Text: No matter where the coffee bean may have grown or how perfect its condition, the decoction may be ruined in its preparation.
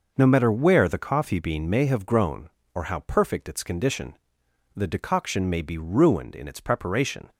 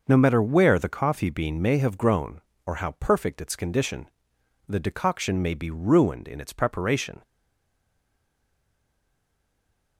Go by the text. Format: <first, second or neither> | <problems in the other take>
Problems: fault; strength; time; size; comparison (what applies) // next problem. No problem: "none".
first | stays silent after the last word; strong; from 7.2 s on; 2.7 s long